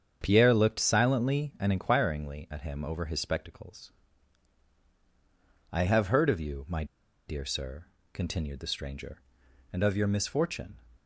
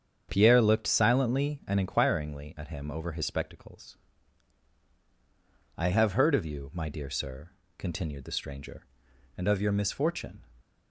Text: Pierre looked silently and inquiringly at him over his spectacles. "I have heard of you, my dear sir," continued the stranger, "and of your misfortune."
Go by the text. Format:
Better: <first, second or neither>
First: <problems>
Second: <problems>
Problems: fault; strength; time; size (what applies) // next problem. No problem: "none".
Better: second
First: starts louder than the rest; strong; until 1.2 s; 7.5 dB // pauses between "my" and "dear"; at 6.8 s; 0.43 s long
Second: starts louder than the rest; strong; until 1.3 s; 7.5 dB